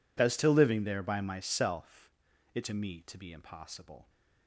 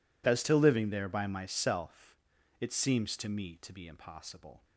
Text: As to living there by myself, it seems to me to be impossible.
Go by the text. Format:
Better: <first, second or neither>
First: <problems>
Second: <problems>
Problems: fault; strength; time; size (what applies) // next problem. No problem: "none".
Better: second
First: skips "seems"; at 2.6 s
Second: none